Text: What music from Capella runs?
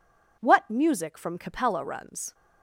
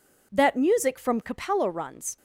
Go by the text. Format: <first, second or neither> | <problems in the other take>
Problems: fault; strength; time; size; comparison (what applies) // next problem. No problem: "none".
first | says "That" for "What"; at 0.3 s